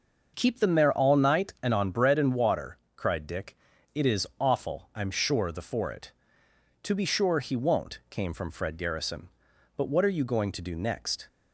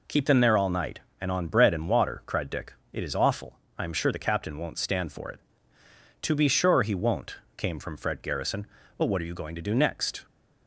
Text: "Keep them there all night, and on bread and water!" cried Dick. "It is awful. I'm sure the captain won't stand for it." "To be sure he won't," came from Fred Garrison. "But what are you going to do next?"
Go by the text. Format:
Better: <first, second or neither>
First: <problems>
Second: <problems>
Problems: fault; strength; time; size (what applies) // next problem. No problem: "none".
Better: second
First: starts louder than the rest; until 1.3 s; 6 dB // skips "captain won't stand"; at 5.6 s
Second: none